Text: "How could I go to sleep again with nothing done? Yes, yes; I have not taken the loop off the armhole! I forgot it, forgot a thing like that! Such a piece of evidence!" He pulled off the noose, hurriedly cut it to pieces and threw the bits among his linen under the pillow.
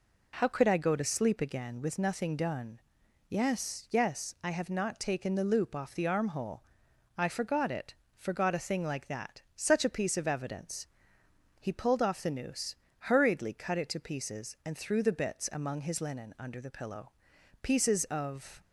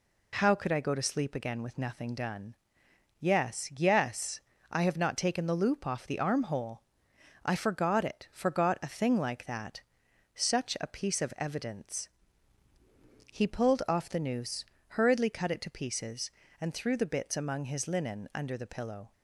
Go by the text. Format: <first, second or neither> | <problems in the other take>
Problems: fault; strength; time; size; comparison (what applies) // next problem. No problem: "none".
second | goes on to say "Pieces of"; noticeable; from 17.6 s on; 0.98 s long